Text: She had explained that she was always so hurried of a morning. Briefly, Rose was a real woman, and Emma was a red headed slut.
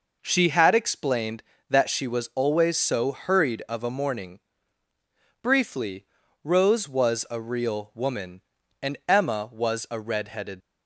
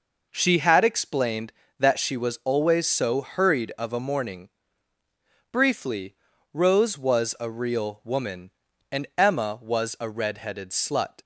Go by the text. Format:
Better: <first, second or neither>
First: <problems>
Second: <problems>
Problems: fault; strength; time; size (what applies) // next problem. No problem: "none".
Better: second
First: stops before "slut"; at 10.6 s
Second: none